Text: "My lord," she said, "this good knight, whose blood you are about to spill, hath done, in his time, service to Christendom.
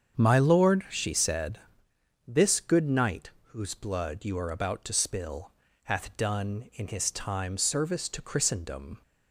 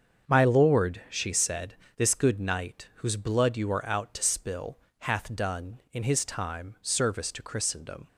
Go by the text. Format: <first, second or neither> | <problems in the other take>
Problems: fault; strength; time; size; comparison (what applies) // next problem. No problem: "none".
first | starts louder than the rest; until 1.3 s; 7 dB; strong in the first // says "out" for "about"; at 3.8 s